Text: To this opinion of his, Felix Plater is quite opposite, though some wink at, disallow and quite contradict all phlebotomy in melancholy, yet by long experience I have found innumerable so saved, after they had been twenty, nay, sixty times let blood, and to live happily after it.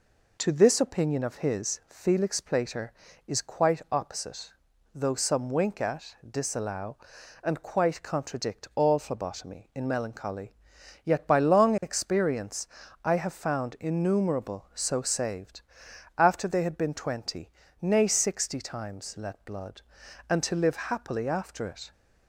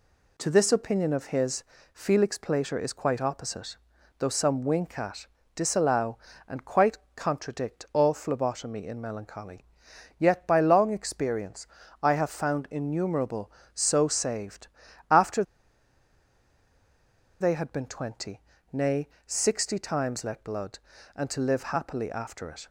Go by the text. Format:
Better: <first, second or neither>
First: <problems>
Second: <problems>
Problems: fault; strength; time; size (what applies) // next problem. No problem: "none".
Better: first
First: pauses between "experience" and "I"; slight; at 12.6 s; 0.36 s long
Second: pauses between "quite" and "contradict"; slight; at 6.9 s; 0.16 s long // pauses between "experience" and "I"; at 11.6 s; 0.38 s long // pauses between "after" and "they"; strong; at 15.4 s; 1.9 s long